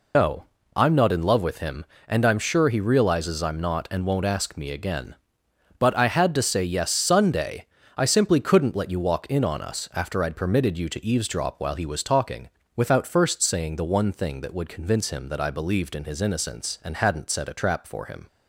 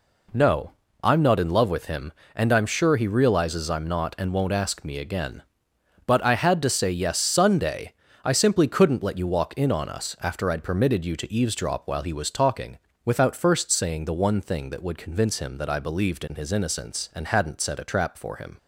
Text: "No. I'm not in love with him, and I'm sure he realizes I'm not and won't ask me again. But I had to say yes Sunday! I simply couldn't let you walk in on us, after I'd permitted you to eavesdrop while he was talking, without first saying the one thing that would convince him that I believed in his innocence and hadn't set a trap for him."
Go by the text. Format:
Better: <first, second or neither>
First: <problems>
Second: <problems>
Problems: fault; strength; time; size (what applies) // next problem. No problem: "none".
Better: second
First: loses the start of "No"; at 0.1 s; 140 ms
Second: none